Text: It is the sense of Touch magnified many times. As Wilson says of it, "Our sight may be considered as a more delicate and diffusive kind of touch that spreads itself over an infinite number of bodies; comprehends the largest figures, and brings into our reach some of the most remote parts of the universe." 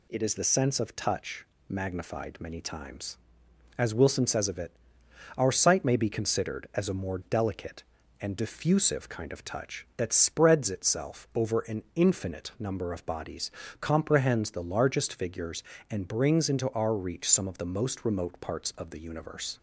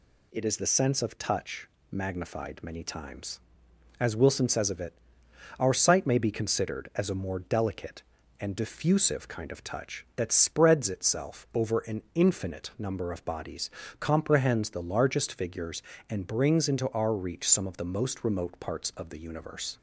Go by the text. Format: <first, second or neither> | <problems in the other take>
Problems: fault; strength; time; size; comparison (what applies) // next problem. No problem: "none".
neither | pauses between "Touch" and "magnified"; slight; the same in both